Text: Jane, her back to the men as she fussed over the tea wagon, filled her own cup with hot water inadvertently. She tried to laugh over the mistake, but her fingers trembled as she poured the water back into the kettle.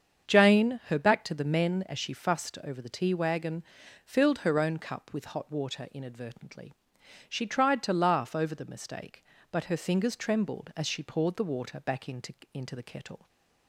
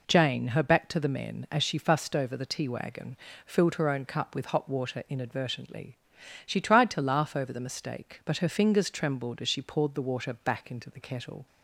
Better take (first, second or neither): second